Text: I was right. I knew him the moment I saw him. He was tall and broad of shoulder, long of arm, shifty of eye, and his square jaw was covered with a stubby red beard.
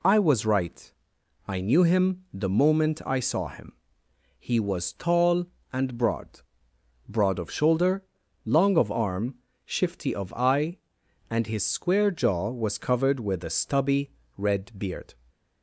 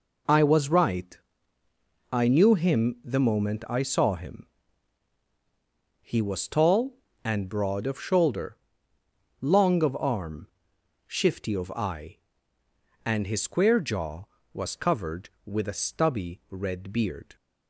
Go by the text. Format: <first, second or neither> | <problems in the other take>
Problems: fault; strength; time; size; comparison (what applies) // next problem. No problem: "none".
second | says "broad" twice; at 7.1 s // pauses between "stubby" and "red"; slight; at 14.1 s; 0.26 s long // stays silent after the last word; slight; from 15.1 s on; 0.5 s long